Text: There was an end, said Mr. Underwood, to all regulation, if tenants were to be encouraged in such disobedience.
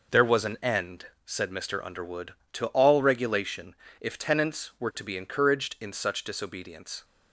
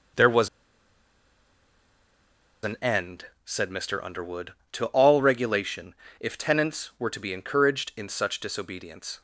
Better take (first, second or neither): first